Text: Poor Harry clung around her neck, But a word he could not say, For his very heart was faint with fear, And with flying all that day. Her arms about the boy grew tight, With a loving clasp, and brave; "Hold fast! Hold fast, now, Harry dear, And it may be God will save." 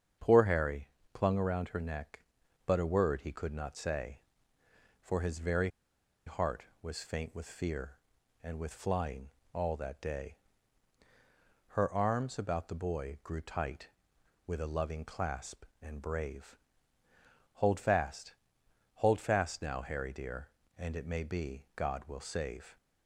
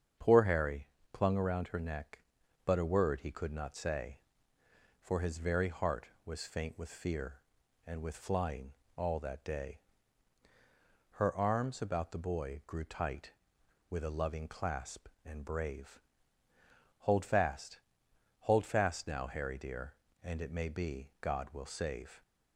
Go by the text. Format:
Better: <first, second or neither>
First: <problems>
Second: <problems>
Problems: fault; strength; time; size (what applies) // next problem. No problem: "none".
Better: second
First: starts louder than the rest; strong; until 1.4 s; 8 dB // pauses between "Harry" and "clung"; slight; at 0.8 s; 0.24 s long // pauses between "very" and "heart"; noticeable; at 5.6 s; 0.58 s long // pauses between "flying" and "all"; slight; at 9.3 s; 0.22 s long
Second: starts louder than the rest; strong; until 1.4 s; 7.5 dB // pauses between "Harry" and "clung"; slight; at 0.8 s; 0.24 s long // pauses between "flying" and "all"; slight; at 8.7 s; 0.22 s long